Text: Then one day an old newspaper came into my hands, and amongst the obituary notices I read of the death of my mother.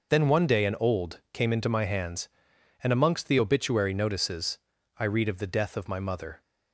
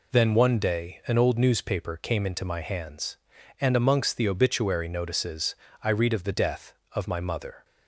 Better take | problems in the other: second | skips "newspaper"; at 1.2 s // pauses between "notices" and "I"; at 4.5 s; 0.40 s long; slight in the second

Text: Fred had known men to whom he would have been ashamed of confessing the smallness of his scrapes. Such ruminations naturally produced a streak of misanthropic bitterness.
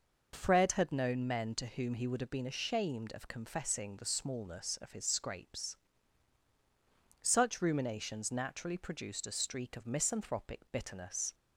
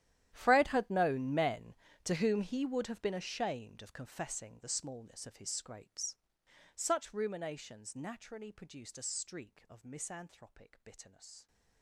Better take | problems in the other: first | gets quieter; strong; throughout; 20 dB

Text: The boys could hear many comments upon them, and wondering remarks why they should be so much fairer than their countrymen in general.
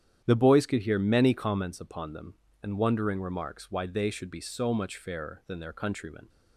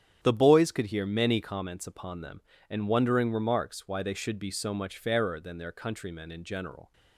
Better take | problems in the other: second | starts louder than the rest; strong; until 1.2 s; 10 dB; strong in the second // stops before "in general"; at 6.2 s

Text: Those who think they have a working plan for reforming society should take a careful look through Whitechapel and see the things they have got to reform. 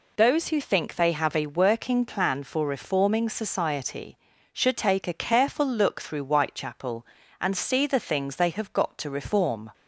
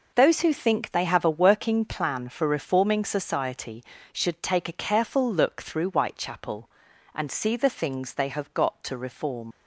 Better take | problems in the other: first | leaves "reform" unfinished; at 9.5 s; 70 ms

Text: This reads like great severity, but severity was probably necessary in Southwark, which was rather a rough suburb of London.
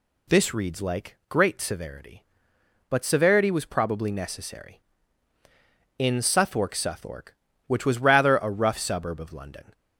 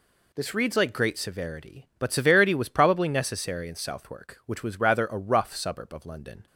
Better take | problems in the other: second | says "Southwark" twice; at 6.7 s

